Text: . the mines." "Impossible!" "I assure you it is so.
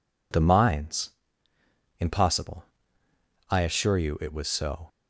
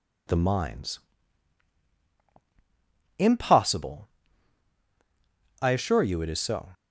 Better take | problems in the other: second | says "was" for "is"; at 4.3 s

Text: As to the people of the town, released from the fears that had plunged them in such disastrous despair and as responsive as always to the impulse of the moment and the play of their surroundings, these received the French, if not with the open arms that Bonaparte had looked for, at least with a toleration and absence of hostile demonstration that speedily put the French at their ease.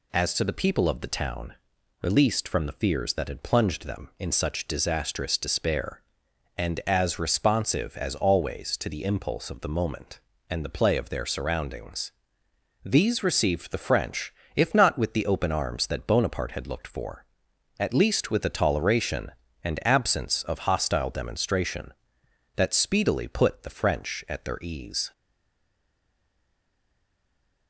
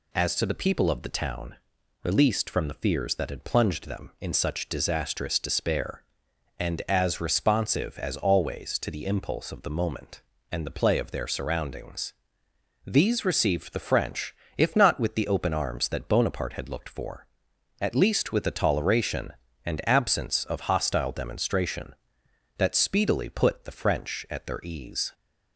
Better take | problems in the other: second | stays silent after the last word; strong; from 25.1 s on; 2.5 s long

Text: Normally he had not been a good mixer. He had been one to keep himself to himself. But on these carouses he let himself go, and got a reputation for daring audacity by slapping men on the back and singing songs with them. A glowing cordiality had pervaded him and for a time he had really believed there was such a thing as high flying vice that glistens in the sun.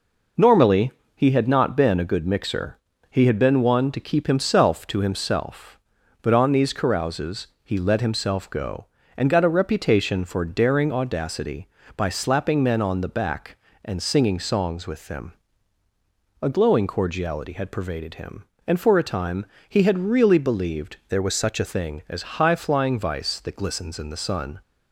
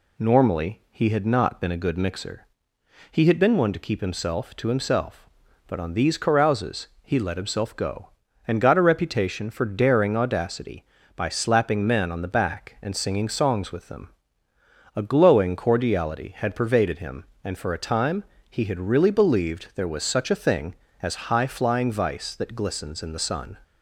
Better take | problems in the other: second | pauses between "Normally" and "he"; slight; at 0.9 s; 0.24 s long // pauses between "carouses" and "he"; slight; at 7.4 s; 0.16 s long // pauses between "time" and "he"; slight; at 19.4 s; 0.24 s long; slight in the second // changes voice from "there" to "a"; from 21.0 to 21.6 s; 0.6 s long

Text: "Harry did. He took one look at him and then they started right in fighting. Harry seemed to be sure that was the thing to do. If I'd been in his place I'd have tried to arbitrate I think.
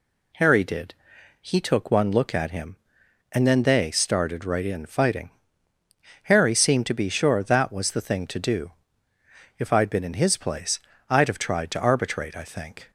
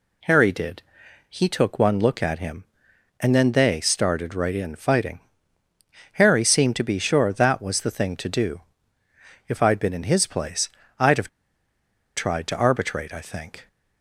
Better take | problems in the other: first | pauses between "place" and "I'd"; slight; at 10.6 s; 0.30 s long; slight in the first // pauses between "have" and "tried"; noticeable; at 11.2 s; 0.88 s long

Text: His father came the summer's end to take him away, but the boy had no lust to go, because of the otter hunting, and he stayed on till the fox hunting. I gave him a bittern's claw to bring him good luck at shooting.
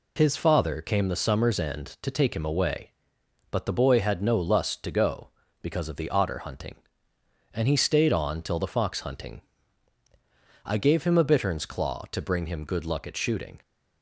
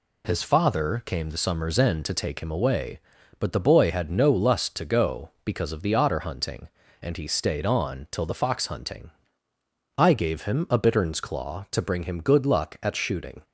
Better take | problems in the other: neither | none

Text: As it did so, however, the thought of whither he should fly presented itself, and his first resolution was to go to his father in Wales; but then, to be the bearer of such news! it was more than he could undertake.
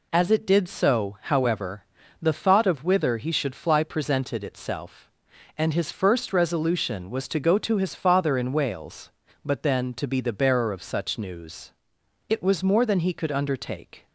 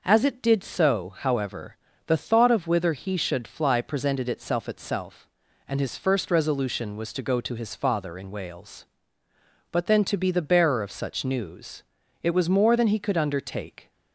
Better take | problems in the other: first | says "itself" twice; at 4.6 s

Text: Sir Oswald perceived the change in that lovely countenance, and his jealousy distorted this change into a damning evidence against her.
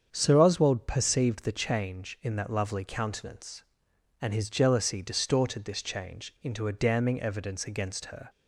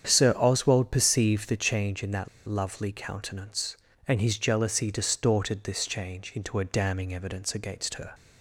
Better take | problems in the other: first | starts louder than the rest; strong; until 1.1 s; 8.5 dB; strong in the first // pauses between "that" and "lovely"; slight; at 2.2 s; 0.20 s long

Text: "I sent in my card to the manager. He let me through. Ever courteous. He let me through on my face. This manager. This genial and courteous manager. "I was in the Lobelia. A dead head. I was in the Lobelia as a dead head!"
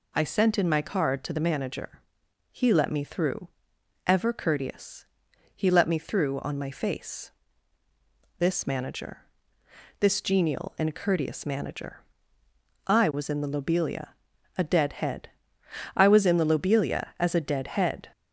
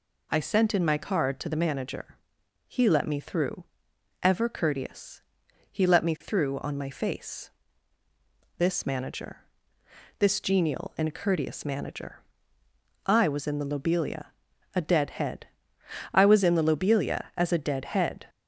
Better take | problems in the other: neither | none

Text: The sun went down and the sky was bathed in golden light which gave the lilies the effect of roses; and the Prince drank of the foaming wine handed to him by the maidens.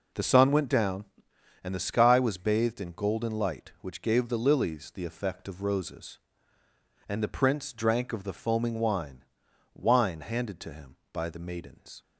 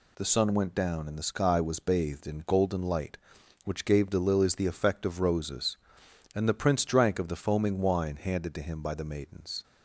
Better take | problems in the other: second | says "wine" twice; at 9.7 s

